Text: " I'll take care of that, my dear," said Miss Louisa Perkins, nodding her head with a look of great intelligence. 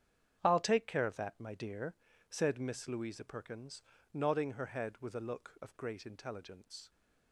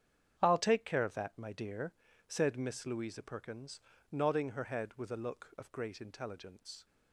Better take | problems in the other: neither | starts louder than the rest; strong; the same in both

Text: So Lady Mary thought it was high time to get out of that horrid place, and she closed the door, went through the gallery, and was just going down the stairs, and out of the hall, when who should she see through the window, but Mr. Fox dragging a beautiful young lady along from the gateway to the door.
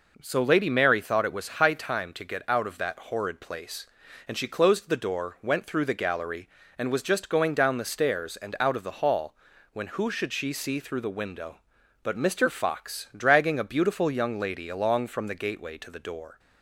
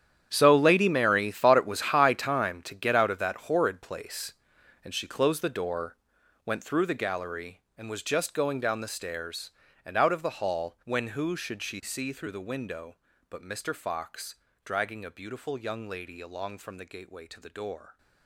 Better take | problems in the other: first | gets quieter; strong; throughout; 16 dB // pauses between "Fox" and "dragging"; slight; at 14.3 s; 0.28 s long

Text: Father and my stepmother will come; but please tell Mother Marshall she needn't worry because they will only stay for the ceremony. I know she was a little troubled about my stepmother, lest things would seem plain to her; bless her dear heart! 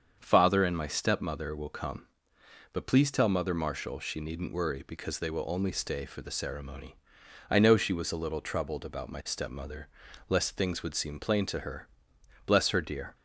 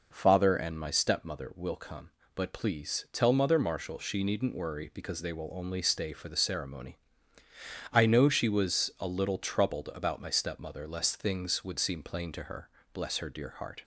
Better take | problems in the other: second | starts louder than the rest; strong; until 1.2 s; 7 dB // stops before "heart"; at 13.1 s

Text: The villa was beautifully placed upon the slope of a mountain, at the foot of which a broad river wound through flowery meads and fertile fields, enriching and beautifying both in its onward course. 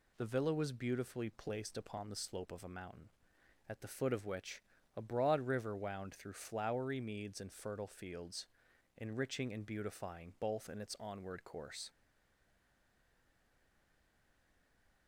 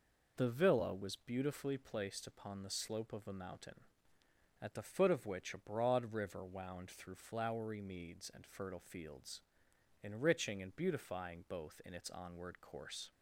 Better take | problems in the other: second | pauses between "which" and "a"; slight; at 4.6 s; 0.34 s long // stays silent after the last word; strong; from 11.8 s on; 3.2 s long

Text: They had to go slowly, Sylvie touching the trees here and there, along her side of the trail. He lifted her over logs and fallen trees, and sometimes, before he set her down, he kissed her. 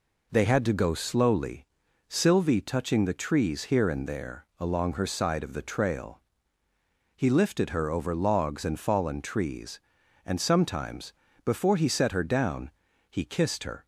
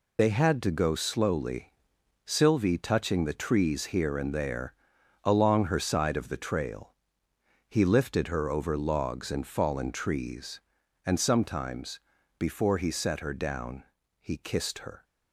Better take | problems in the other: first | loses the start of "They"; at 0.1 s; 50 ms

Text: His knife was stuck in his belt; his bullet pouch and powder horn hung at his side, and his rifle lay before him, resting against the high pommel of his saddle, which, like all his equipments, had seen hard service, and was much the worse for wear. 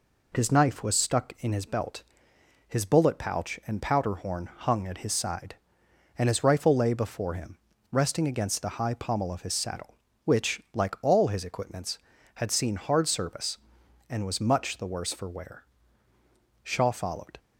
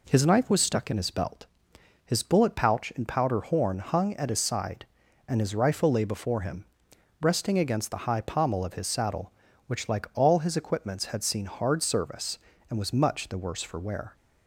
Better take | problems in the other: second | goes on to say "Shaw followed"; noticeable; from 16.6 s on; 0.74 s long

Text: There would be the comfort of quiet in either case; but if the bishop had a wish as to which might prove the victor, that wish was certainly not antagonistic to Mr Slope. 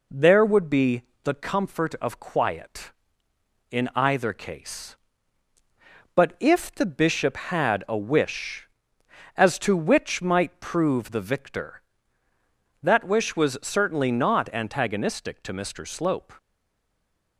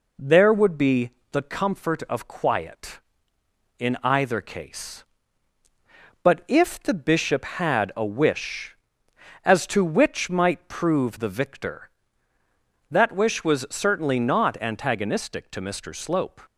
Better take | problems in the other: second | pauses between "be" and "the"; slight; at 1.0 s; 0.22 s long; slight in the second // stays silent after the last word; from 16.3 s on; 1.0 s long

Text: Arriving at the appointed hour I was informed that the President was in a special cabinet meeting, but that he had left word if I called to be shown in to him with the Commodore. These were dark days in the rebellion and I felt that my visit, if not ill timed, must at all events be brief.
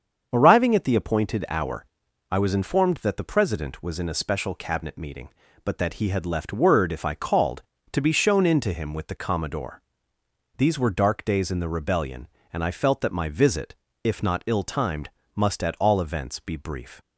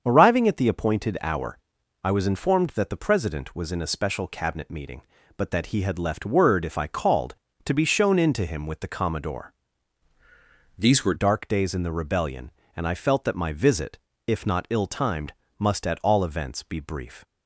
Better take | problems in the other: first | starts louder than the rest; until 1.0 s; 7 dB; also in the first // pauses between "hour" and "I"; noticeable; at 1.5 s; 0.48 s long; noticeable in the first // changes voice from "These" to "were"; from 10.7 to 11.1 s; 0.4 s long

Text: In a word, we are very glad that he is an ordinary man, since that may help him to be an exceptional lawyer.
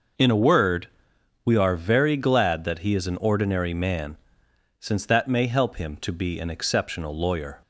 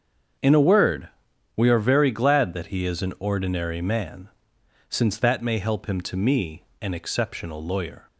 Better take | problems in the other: first | starts louder than the rest; until 1.8 s; 7 dB // says "me" for "be"; at 6.1 s

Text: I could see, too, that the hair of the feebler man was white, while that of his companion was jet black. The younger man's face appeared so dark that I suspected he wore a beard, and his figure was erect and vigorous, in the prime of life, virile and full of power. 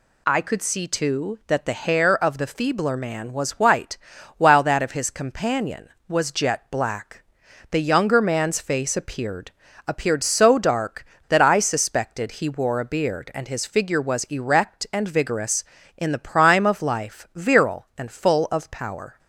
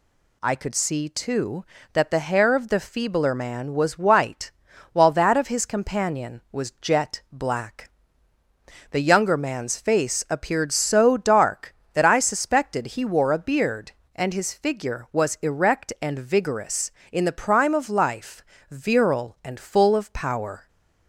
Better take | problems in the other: second | says "appeared" twice; at 9.8 s

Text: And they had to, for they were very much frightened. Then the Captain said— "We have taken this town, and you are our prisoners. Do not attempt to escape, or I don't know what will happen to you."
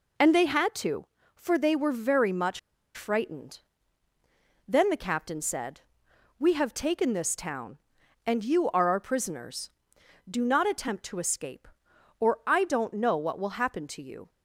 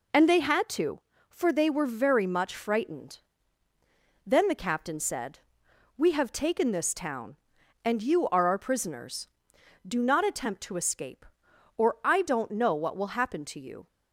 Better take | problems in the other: second | pauses between "much" and "frightened"; slight; at 2.5 s; 0.35 s long

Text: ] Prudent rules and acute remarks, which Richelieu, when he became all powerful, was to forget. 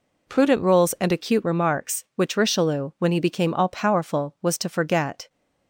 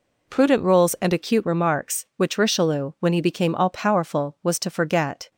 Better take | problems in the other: neither | none

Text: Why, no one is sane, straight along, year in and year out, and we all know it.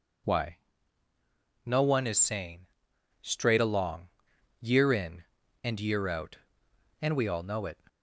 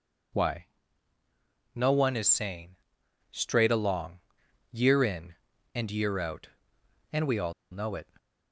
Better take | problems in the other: first | pauses between "all" and "know"; slight; at 7.5 s; 0.18 s long

